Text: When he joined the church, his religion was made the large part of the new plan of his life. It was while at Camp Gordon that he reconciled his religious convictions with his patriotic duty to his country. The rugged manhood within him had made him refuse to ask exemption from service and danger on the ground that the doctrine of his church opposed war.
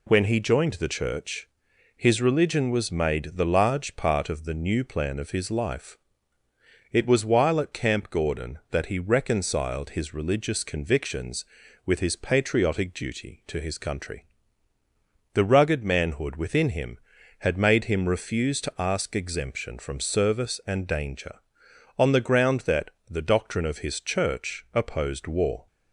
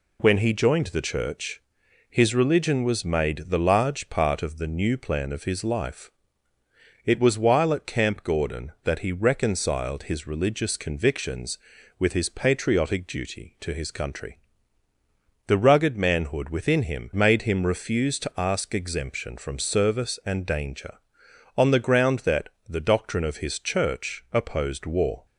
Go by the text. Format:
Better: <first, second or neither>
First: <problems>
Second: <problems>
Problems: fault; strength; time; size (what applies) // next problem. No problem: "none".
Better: first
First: pauses between "that" and "the"; slight; at 22.9 s; 0.20 s long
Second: skips "had"; at 17.1 s // pauses between "that" and "the"; slight; at 22.4 s; 0.20 s long